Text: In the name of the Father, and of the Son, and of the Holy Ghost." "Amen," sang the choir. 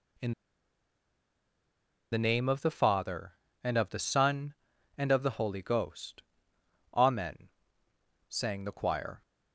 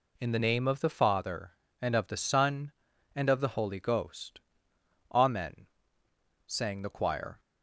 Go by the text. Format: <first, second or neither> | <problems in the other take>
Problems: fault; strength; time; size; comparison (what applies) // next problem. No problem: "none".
second | pauses between "In" and "the"; strong; at 0.3 s; 1.8 s long